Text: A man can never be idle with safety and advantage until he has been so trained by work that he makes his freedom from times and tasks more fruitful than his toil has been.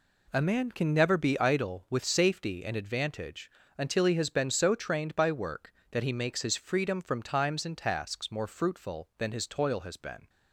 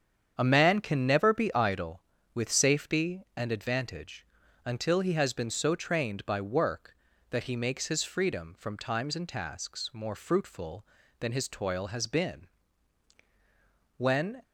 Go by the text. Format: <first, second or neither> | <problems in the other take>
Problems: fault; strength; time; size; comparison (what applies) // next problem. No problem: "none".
first | starts louder than the rest; strong; until 1.3 s; 8 dB // pauses between "advantage" and "until"; at 4.2 s; 0.40 s long; slight in the first // goes on to say "When"; slight; from 13.9 s on; 0.44 s long